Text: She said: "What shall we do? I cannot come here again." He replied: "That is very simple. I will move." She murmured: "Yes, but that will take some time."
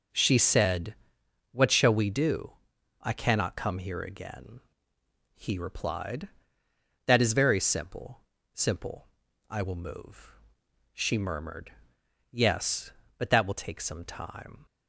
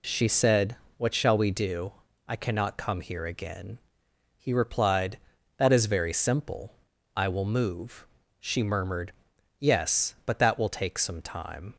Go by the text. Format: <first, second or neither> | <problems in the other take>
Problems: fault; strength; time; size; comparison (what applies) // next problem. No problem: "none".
second | says "simple" twice; at 8.5 s